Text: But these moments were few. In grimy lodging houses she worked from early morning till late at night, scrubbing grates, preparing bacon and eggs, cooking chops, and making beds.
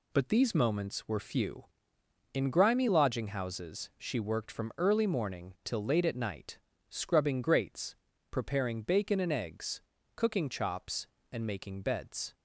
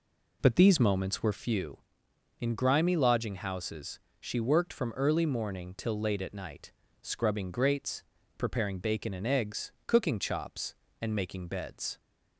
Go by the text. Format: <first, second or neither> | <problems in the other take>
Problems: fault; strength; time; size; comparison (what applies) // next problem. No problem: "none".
first | starts louder than the rest; slight; until 1.5 s; 3 dB // pauses between "houses" and "she"; slight; at 3.9 s; 0.20 s long